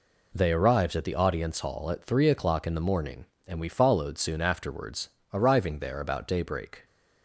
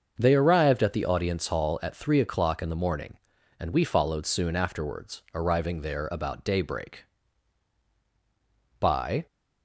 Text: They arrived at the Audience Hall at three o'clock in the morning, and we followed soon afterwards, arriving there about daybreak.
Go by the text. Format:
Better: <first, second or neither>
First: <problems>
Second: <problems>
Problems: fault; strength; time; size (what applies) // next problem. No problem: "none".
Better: first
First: none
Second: starts louder than the rest; until 1.2 s; 6.5 dB // goes on to say "By"; slight; from 8.7 s on; 0.48 s long